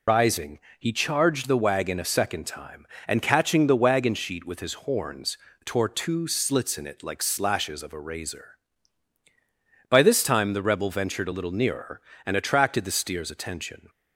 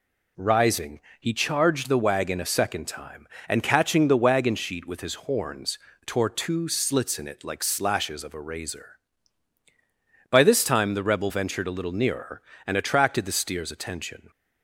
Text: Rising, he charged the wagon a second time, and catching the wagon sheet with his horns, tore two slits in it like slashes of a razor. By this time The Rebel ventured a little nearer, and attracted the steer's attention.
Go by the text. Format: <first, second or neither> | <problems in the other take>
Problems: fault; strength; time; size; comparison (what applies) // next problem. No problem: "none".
second | loses the start of "Rising"; at 0.0 s; 125 ms